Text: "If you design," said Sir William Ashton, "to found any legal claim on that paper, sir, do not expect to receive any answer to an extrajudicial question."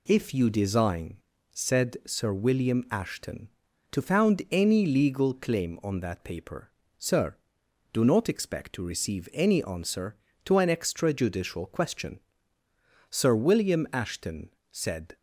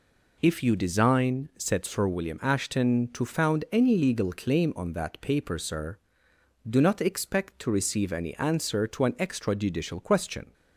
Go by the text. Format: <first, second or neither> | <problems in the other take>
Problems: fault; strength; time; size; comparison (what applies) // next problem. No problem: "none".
second | goes on to say "Sir William Ashton said"; strong; from 13.1 s on; 2.0 s long